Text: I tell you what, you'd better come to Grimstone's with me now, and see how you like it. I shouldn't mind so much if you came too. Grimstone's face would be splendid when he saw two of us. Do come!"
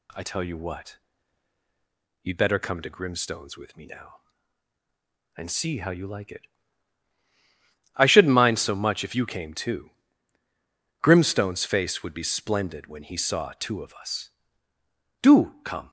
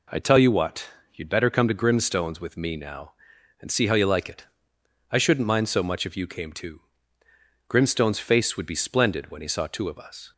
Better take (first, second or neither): first